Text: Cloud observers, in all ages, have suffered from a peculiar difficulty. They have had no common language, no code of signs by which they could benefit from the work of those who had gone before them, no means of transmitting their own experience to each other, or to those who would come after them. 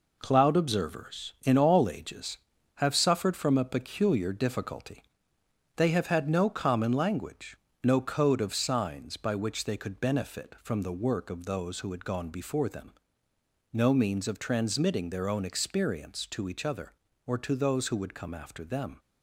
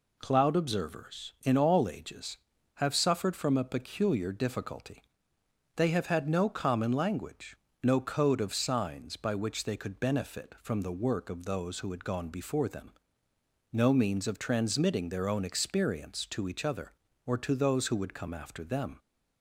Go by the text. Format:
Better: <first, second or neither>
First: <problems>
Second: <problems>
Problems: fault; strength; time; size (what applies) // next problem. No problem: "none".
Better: second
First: gets quieter; throughout; 6.5 dB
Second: none